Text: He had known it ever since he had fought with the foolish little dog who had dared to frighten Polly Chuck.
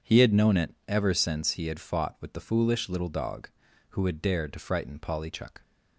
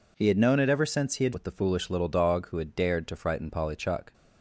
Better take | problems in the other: first | skips "fought"; at 1.3 s

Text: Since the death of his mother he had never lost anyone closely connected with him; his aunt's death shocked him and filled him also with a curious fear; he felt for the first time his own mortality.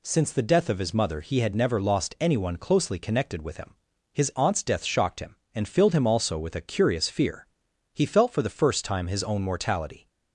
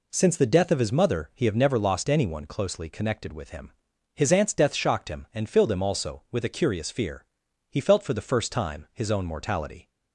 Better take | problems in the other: first | says "have" for "had"; at 1.4 s

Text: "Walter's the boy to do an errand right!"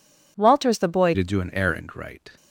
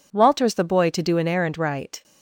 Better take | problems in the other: second | changes voice at "to"; from 1.1 s on; 1.2 s long

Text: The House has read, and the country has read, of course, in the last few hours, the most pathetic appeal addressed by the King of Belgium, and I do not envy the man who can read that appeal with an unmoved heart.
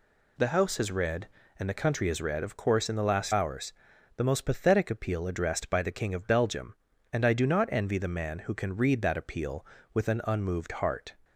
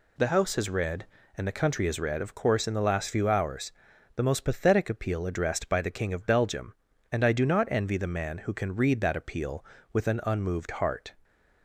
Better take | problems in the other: second | skips "few"; at 3.3 s

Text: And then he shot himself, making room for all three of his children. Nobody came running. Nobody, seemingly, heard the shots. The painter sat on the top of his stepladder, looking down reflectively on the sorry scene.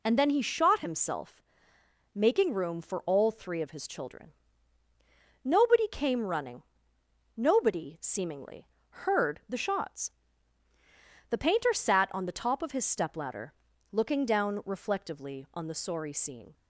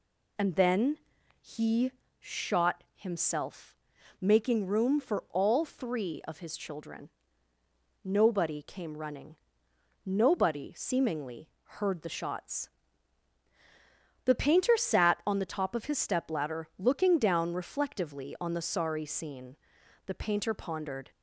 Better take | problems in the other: first | pauses between "then" and "he"; at 0.9 s; 0.42 s long // pauses between "he" and "shot"; slight; at 1.9 s; 0.30 s long // goes on to say "The painter pondered"; noticeable; from 20.0 s on; 1.0 s long

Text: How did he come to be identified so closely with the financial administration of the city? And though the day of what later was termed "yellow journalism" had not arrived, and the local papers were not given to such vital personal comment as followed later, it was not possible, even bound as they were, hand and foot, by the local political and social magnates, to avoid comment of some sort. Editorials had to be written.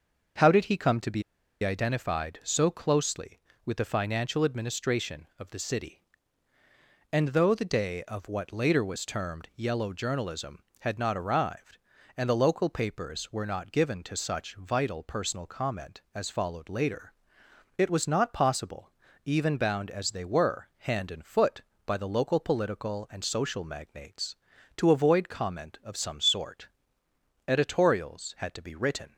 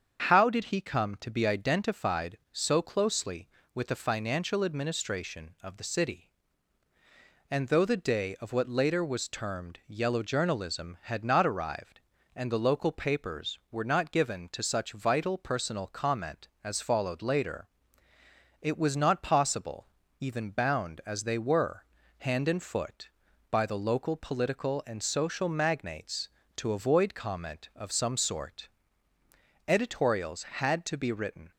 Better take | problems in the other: second | starts louder than the rest; until 1.7 s; 6 dB; strong in the second // pauses between "be" and "identified"; at 1.2 s; 0.40 s long

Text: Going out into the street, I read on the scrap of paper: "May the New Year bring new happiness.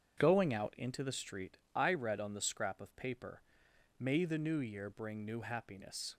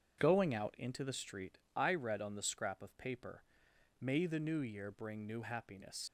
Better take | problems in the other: first | starts louder than the rest; strong; until 1.2 s; 7.5 dB; strong in the first // leaves "happiness" unfinished; at 6.0 s; 85 ms

